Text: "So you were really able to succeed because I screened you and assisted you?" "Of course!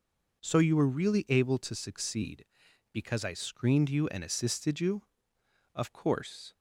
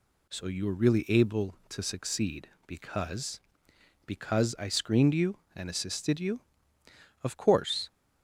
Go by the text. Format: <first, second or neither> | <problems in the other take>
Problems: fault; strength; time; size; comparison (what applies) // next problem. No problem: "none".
first | says "because" twice; at 4.0 s